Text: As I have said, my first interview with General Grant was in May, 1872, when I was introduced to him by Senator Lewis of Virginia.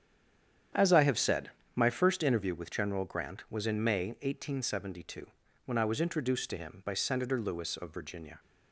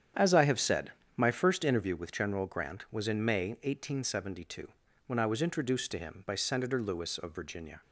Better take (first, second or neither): second